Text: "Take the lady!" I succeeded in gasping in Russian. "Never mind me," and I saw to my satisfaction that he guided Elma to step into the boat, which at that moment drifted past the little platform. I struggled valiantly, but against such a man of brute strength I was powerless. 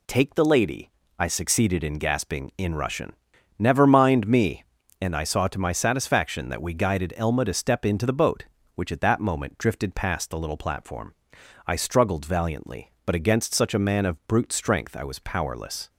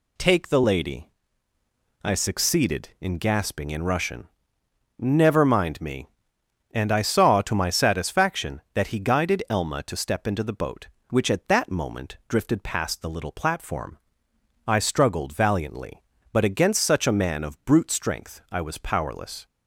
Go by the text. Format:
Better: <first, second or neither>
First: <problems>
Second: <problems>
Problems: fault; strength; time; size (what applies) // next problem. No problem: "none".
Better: second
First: says "we" for "he"; at 6.6 s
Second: none